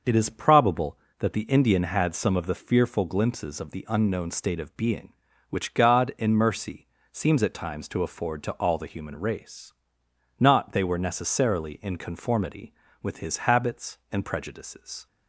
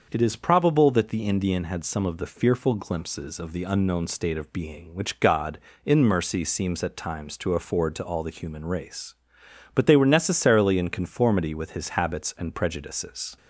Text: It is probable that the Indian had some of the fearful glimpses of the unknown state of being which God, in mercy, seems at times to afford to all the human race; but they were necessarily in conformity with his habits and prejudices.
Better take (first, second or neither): second